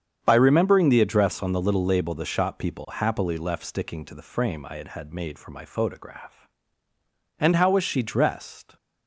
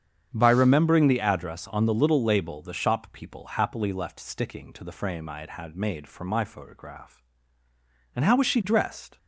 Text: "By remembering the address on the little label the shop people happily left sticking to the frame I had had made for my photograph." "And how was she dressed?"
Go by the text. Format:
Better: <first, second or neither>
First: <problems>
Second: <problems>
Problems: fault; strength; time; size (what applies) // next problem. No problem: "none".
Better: neither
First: starts louder than the rest; strong; until 1.2 s; 8 dB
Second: starts louder than the rest; strong; until 1.3 s; 8 dB